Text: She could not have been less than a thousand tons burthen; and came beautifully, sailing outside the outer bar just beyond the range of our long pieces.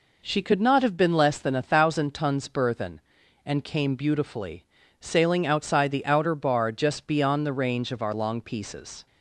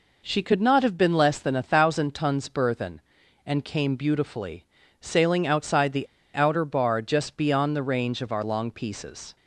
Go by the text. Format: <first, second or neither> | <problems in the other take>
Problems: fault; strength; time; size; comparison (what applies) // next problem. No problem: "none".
first | pauses between "the" and "outer"; slight; at 6.0 s; 0.27 s long